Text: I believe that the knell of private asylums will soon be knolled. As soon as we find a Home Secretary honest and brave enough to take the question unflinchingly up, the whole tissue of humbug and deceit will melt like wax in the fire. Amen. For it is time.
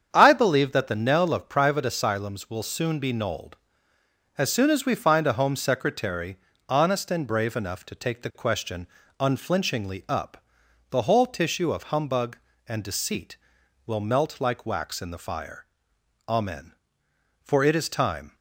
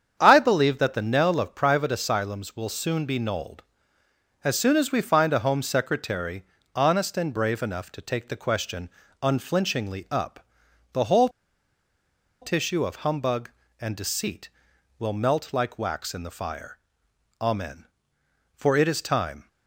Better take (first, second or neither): first